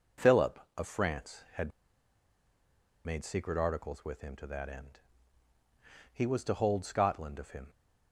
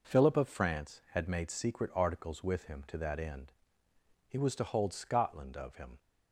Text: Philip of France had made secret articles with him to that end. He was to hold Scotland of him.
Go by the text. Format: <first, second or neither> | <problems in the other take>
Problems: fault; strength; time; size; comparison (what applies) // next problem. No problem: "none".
second | pauses between "had" and "made"; strong; at 1.7 s; 1.3 s long